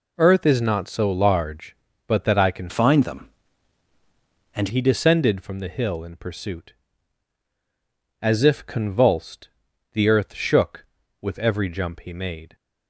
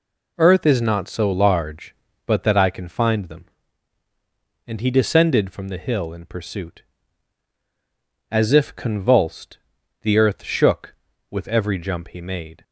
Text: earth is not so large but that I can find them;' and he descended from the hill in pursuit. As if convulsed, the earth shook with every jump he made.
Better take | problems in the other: second | changes voice from "find" to "and"; from 2.6 to 4.6 s; 2.0 s long

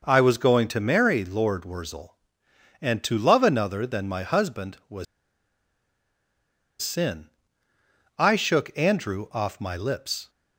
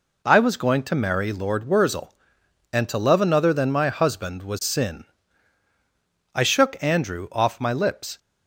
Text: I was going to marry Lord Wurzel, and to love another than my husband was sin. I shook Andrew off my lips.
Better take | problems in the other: second | pauses between "was" and "sin"; strong; at 5.0 s; 1.7 s long

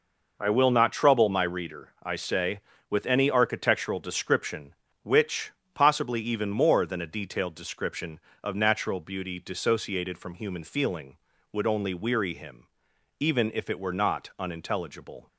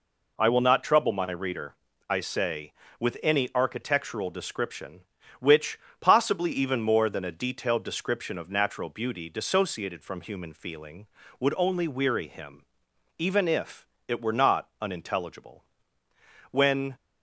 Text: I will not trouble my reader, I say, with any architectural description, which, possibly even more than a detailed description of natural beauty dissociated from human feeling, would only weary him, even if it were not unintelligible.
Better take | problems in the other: first | pauses between "if" and "it"; slight; at 13.8 s; 0.20 s long // goes on to say "When"; slight; from 16.5 s on; 0.44 s long

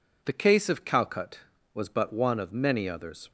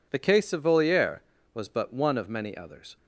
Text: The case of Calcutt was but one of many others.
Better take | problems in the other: first | says "Voliere" for "Calcutt"; at 0.6 s

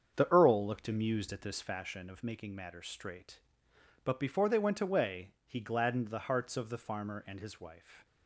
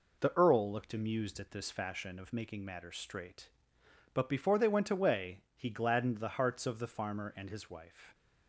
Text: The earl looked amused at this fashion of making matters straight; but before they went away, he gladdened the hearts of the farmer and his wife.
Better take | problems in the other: second | starts louder than the rest; strong; until 1.7 s; 7 dB

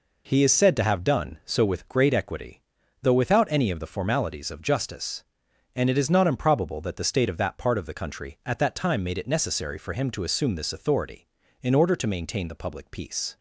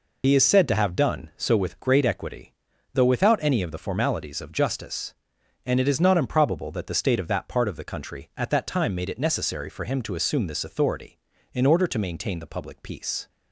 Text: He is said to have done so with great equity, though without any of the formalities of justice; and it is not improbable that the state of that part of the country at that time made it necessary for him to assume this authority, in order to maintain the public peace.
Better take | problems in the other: first | loses the start of "He"; at 0.2 s; 75 ms

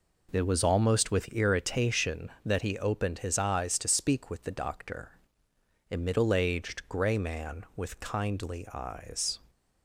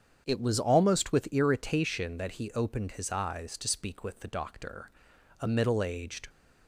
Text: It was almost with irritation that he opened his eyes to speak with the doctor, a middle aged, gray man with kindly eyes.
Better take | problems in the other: first | starts louder than the rest; strong; until 1.2 s; 8 dB // stops before "gray man with kindly eyes"; at 6.2 s

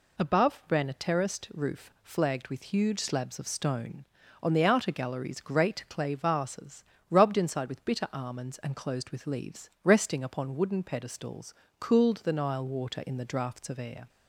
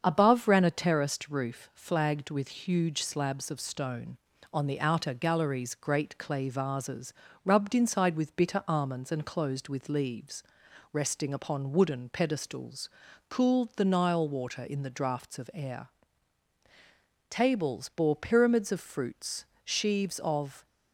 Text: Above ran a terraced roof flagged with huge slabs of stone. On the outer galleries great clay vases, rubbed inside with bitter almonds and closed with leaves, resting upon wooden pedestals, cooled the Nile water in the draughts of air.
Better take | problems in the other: first | starts louder than the rest; strong; until 1.0 s; 7 dB // goes on to say "Tables bore pyramids of fruits sheaves of"; strong; from 17.2 s on; 3.3 s long

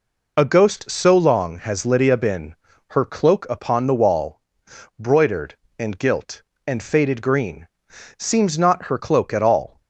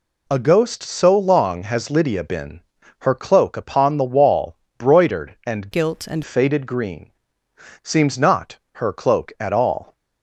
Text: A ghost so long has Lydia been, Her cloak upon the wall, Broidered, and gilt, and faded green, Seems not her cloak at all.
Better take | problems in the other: first | changes voice from "gilt" to "and"; from 5.7 to 6.2 s; 0.5 s long

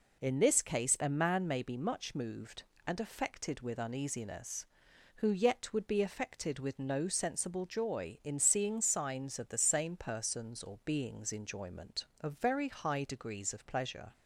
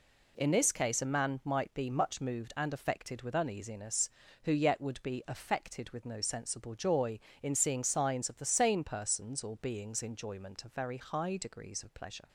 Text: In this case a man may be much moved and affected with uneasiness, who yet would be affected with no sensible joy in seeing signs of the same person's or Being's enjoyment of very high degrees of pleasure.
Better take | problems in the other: first | says "might" for "may"; at 1.4 s

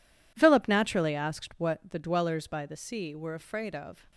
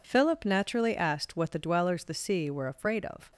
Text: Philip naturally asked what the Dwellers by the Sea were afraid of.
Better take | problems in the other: first | skips "by"; at 2.0 s

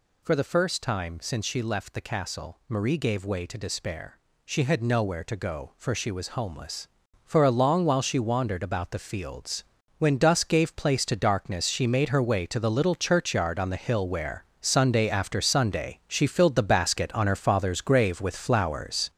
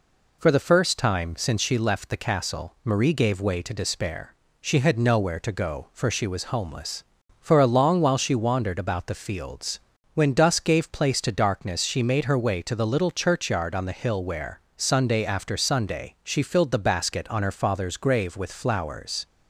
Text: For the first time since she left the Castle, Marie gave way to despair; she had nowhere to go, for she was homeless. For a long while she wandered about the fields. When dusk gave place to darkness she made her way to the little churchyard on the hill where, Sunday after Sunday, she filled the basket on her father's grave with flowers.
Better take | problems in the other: second | gets louder; throughout; 6.5 dB

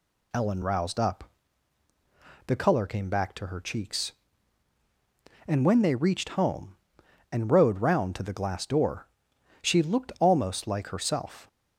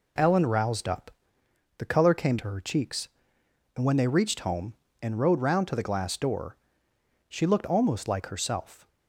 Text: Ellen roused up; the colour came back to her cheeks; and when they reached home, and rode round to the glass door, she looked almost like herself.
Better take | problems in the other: first | skips "back"; at 2.3 s

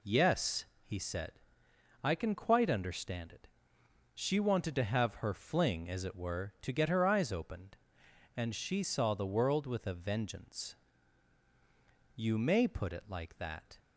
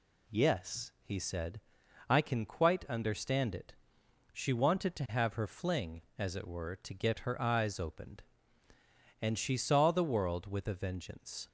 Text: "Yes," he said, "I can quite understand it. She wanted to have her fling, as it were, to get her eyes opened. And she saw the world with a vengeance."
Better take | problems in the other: second | goes on to say "You may put it like that"; from 12.1 s on; 1.6 s long

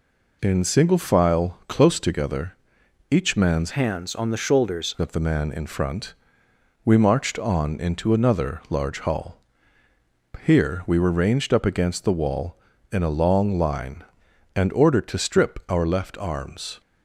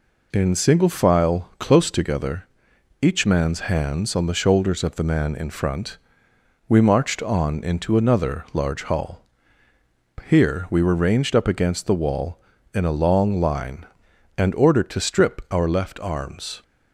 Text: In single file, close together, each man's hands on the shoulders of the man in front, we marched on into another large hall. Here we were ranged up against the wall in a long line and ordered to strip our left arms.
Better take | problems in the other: second | changes voice from "hands" to "shoulders"; from 3.7 to 4.9 s; 1.2 s long

